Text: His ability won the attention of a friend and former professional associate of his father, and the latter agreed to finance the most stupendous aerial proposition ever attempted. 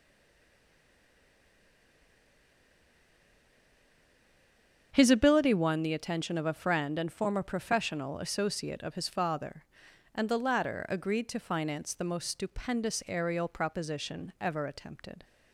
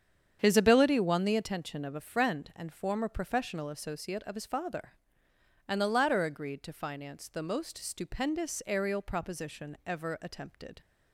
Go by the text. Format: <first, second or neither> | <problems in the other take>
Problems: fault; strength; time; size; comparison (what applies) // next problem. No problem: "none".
second | stays silent before the first word; strong; until 4.9 s; 4.9 s long // starts louder than the rest; strong; until 5.9 s; 7.5 dB; strong in the second